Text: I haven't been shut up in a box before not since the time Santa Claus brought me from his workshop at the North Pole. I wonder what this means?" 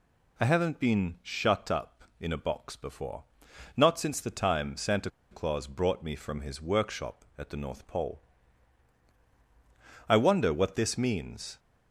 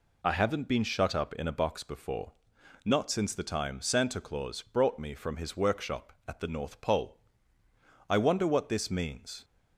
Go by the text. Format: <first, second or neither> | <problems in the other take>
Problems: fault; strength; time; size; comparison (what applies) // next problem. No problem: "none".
second | pauses between "before" and "not"; noticeable; at 3.2 s; 0.50 s long; noticeable in the second // pauses between "Santa" and "Claus"; slight; at 5.0 s; 0.22 s long